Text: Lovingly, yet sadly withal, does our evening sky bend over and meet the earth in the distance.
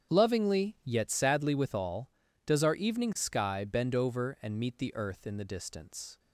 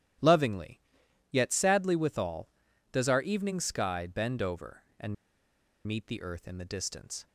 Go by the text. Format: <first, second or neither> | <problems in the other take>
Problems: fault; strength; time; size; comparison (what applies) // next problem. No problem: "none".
first | starts louder than the rest; strong; until 1.7 s; 12 dB; strong in the first // pauses between "and" and "meet"; noticeable; at 5.1 s; 0.71 s long